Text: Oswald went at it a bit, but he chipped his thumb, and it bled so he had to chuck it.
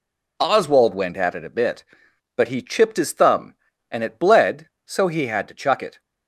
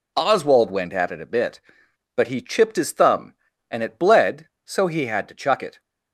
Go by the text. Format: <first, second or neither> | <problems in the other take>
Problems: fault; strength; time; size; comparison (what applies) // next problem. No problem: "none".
neither | none